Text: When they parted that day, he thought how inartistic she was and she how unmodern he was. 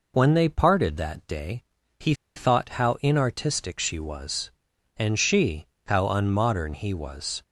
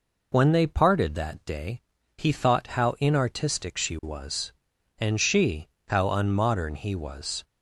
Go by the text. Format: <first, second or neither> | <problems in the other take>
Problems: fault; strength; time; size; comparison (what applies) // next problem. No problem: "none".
second | pauses between "he" and "thought"; slight; at 2.1 s; 0.22 s long // pauses between "she" and "how"; slight; at 5.6 s; 0.20 s long; slight in the second